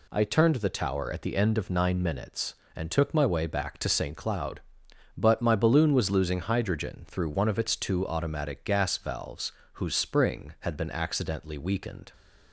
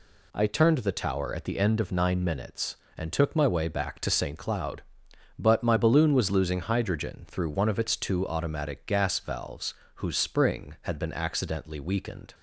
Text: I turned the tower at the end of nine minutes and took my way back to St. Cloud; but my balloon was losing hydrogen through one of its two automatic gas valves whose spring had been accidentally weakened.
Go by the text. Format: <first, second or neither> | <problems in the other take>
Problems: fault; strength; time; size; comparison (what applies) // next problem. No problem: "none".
neither | pauses between "valves" and "whose"; slight; the same in both